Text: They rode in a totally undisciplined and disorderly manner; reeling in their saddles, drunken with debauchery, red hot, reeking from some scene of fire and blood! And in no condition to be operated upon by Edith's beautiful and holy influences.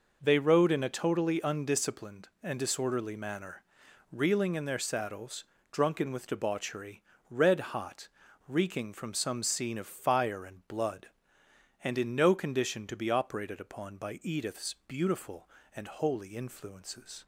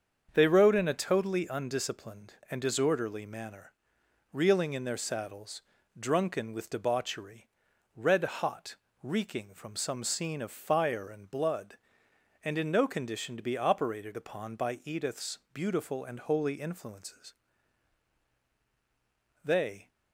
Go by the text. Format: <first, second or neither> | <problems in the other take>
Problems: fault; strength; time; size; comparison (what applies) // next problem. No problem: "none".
first | starts louder than the rest; until 1.3 s; 7 dB // goes on to say "They"; slight; from 19.4 s on; 0.46 s long